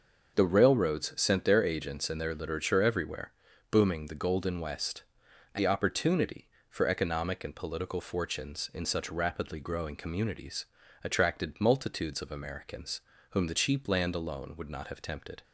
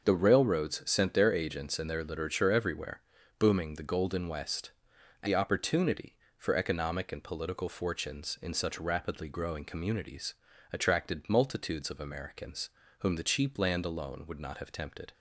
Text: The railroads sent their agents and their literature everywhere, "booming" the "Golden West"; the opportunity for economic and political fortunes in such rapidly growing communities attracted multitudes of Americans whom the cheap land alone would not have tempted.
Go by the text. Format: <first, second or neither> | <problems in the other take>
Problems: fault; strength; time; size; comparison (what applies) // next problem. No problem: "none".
neither | starts louder than the rest; noticeable; the same in both // pauses between "communities" and "attracted"; the same in both // pauses between "Americans" and "whom"; slight; the same in both